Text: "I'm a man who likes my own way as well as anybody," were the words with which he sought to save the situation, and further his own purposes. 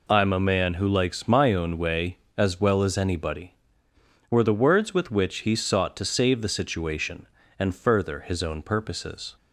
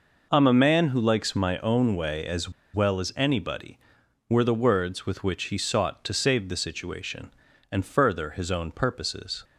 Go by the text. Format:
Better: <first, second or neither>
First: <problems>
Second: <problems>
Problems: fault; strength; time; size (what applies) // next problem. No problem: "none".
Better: first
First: none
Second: pauses between "as" and "well"; slight; at 2.5 s; 0.23 s long